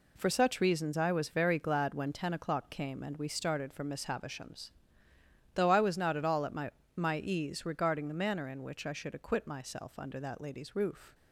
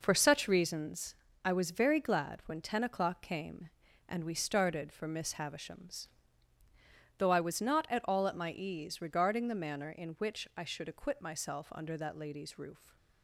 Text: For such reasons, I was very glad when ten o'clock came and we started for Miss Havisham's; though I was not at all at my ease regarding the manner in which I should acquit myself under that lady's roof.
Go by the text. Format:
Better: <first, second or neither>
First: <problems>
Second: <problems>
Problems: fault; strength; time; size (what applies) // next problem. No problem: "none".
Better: second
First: says "my" twice; at 6.9 s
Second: none